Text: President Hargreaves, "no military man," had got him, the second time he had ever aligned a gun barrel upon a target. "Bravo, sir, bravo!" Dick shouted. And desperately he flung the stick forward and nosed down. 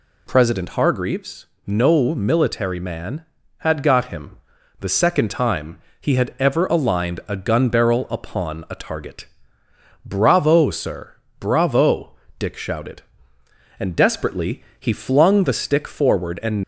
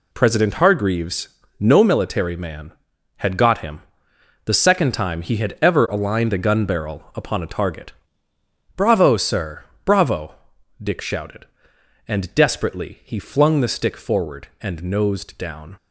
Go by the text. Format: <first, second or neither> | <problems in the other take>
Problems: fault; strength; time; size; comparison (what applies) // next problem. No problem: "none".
second | pauses between "time" and "he"; slight; at 5.7 s; 0.24 s long // stops before "nosed down"; at 16.6 s